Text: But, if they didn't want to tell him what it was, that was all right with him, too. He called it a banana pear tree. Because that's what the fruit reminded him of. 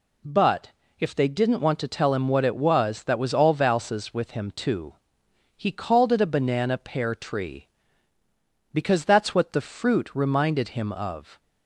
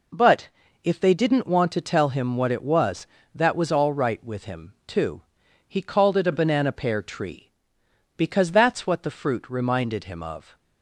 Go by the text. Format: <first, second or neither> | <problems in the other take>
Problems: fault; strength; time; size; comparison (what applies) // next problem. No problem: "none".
second | says "valses" for "right"; at 3.5 s